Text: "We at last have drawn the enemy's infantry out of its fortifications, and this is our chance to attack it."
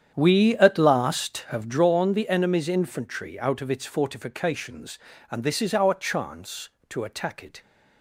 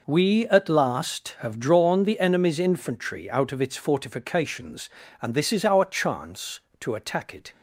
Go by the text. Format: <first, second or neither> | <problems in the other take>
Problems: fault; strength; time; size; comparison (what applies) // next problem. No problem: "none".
second | starts louder than the rest; strong; until 1.7 s; 9 dB